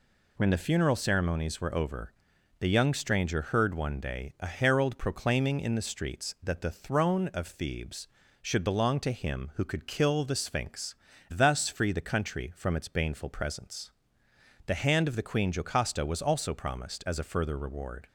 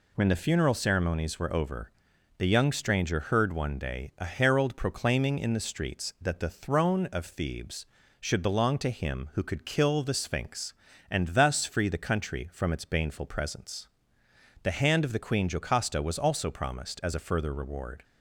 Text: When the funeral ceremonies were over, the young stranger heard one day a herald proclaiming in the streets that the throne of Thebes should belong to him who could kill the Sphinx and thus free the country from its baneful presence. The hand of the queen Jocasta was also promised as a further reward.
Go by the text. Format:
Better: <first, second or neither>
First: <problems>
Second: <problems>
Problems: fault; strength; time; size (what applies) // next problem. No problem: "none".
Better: second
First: skips "and"; at 11.1 s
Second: none